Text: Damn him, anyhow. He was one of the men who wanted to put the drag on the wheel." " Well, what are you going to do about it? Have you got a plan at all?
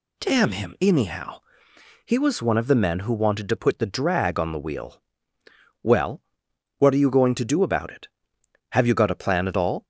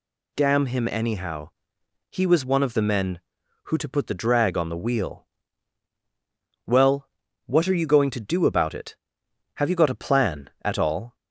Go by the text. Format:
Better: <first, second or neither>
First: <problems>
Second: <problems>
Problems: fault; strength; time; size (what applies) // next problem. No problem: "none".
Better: first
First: none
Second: skips "wanted"; at 3.7 s